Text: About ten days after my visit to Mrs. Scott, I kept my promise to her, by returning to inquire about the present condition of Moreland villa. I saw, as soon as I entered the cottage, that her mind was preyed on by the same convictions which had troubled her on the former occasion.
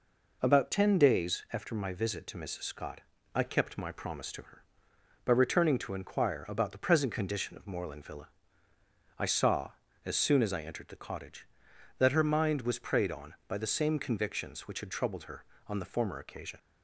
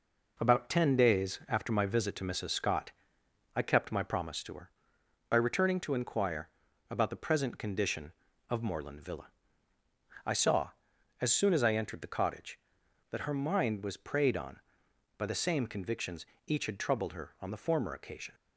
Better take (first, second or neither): first